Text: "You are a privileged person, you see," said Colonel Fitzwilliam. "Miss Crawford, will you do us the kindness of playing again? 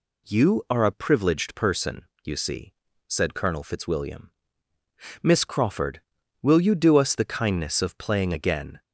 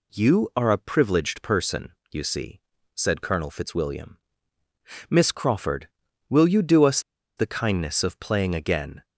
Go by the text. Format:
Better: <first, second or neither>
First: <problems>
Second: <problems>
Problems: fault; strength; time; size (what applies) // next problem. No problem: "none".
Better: first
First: none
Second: pauses between "us" and "the"; at 6.9 s; 0.37 s long